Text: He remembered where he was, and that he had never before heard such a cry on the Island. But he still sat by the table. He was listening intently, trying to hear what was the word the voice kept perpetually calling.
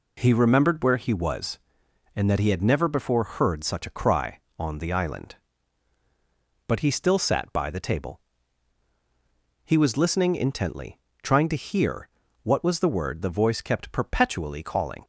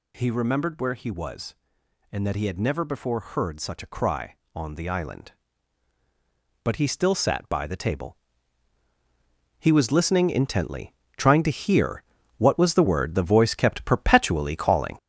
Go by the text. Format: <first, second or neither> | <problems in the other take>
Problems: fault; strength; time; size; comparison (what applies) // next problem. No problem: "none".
first | gets louder; throughout; 6 dB // pauses between "hear" and "what"; slight; at 12.0 s; 0.32 s long; slight in the first